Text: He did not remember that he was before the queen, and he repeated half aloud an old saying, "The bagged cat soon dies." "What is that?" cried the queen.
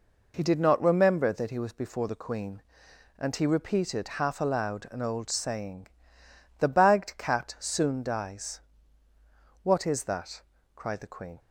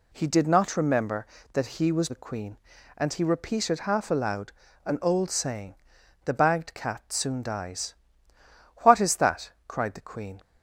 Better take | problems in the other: first | skips "before"; at 2.0 s // pauses between "aloud" and "an"; slight; at 4.5 s; 0.32 s long

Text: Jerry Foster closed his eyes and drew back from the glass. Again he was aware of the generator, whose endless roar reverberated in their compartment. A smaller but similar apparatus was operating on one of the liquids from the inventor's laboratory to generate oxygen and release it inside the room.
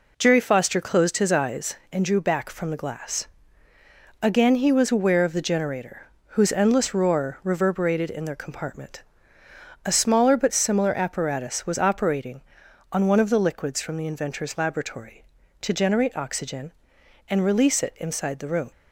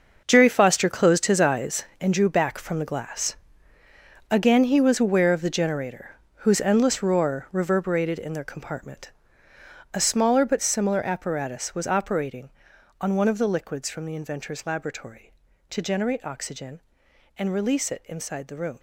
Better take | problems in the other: first | gets quieter; strong; throughout; 12 dB

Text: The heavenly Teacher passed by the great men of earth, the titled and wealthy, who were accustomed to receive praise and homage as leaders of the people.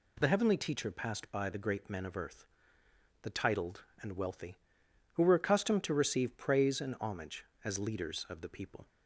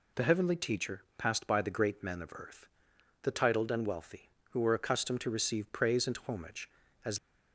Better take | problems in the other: first | stops before "leaders of the people"; at 7.1 s

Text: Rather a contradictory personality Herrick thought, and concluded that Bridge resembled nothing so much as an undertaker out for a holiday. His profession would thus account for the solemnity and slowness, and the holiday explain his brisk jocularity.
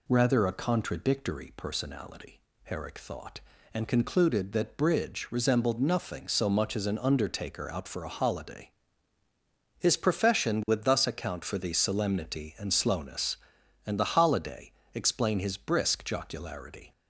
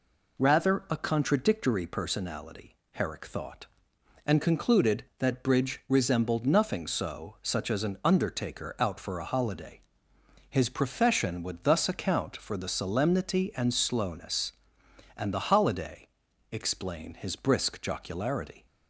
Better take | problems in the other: first | pauses between "personality" and "Herrick"; slight; at 2.7 s; 0.18 s long; slight in the first // says "such" for "much"; at 7.4 s // pauses between "holiday" and "explain"; at 16.0 s; 0.44 s long; slight in the first

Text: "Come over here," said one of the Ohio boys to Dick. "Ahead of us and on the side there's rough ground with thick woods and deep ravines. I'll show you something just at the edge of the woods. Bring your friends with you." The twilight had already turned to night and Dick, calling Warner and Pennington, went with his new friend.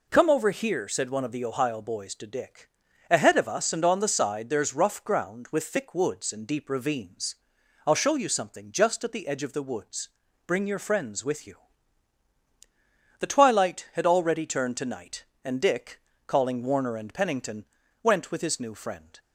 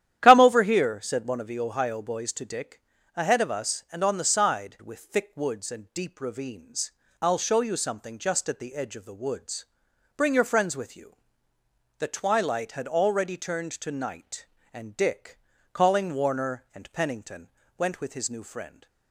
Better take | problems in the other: first | starts louder than the rest; strong; until 1.2 s; 11 dB // skips "there's rough ground"; at 4.7 s

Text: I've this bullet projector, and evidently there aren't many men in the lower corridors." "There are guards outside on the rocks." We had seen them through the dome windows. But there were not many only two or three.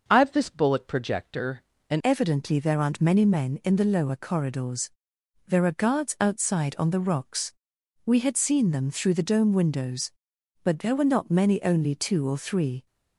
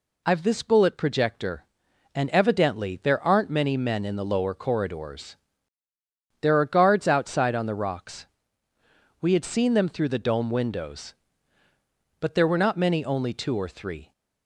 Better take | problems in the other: second | starts louder than the rest; noticeable; until 1.0 s; 6 dB // changes voice at "evidently"; from 2.0 s on; 10.8 s long

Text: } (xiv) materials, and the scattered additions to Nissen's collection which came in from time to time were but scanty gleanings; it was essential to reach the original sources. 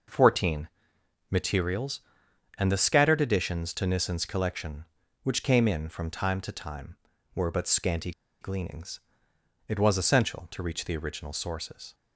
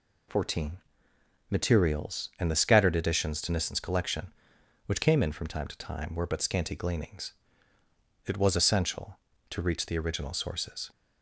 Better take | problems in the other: second | pauses between "scanty" and "gleanings"; slight; at 8.1 s; 0.30 s long

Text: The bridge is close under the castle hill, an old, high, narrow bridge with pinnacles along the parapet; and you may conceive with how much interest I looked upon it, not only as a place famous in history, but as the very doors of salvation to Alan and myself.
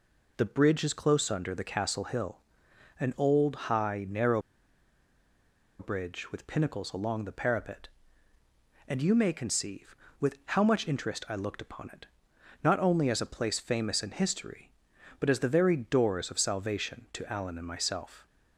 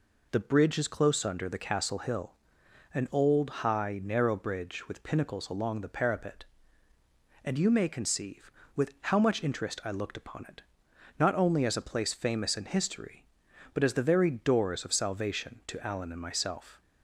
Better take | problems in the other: second | pauses between "narrow" and "bridge"; strong; at 4.4 s; 1.3 s long

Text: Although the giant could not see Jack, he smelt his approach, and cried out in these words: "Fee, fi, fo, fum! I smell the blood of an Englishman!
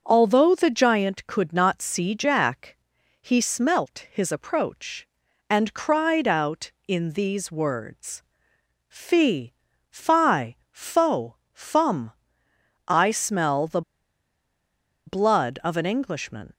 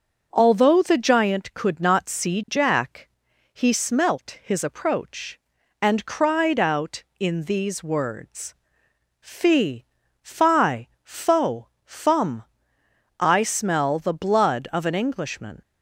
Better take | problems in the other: second | pauses between "the" and "blood"; strong; at 13.8 s; 1.2 s long

